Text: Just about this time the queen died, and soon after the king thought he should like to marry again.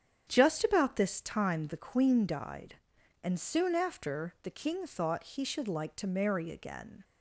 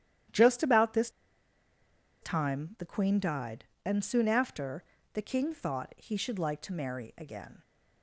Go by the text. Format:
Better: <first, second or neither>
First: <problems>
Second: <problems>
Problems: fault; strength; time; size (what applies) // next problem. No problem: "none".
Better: first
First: starts louder than the rest; strong; until 1.2 s; 8.5 dB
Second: starts louder than the rest; strong; until 2.4 s; 11 dB // pauses between "this" and "time"; at 1.0 s; 1.1 s long // pauses between "after" and "the"; slight; at 4.8 s; 0.30 s long